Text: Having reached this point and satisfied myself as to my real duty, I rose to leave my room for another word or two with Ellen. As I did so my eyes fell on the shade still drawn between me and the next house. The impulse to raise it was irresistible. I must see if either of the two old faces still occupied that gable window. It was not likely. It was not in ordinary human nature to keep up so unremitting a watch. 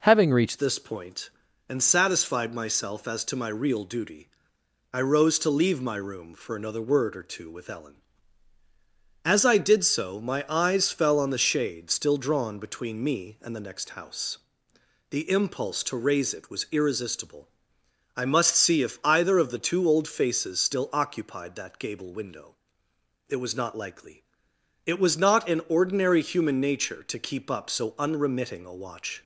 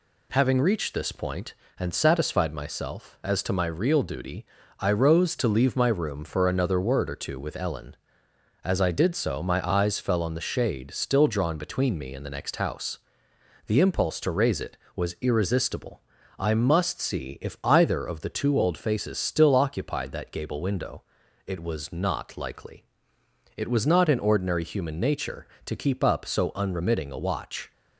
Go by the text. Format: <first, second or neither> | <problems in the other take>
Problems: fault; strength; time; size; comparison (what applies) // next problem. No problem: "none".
second | changes voice at "this"; from 0.5 s on; 28.7 s long